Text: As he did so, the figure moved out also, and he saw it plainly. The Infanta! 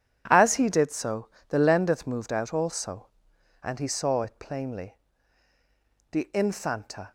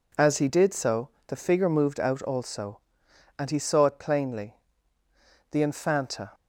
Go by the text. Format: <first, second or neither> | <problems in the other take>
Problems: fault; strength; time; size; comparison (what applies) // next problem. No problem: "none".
second | says "lendeth" for "figure"; at 1.5 s